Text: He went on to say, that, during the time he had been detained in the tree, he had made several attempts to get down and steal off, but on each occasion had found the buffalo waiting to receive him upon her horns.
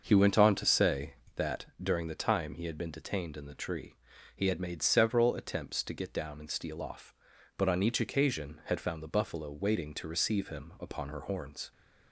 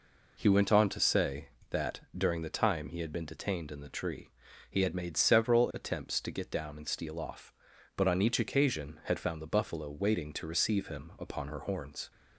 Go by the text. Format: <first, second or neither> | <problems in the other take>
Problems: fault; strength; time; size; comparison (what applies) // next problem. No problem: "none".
second | starts louder than the rest; noticeable; until 1.5 s; 6 dB